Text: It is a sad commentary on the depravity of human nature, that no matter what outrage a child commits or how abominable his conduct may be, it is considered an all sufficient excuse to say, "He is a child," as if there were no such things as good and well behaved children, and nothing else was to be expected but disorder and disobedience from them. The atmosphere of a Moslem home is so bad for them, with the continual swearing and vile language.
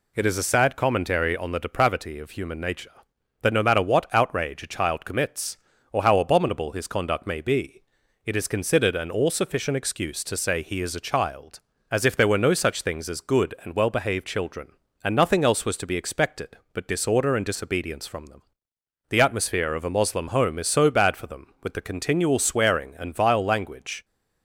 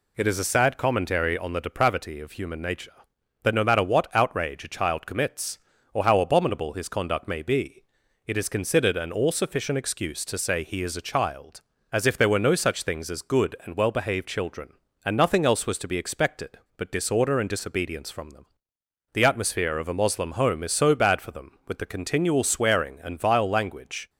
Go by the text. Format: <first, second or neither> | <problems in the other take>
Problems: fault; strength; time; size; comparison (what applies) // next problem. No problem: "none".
neither | none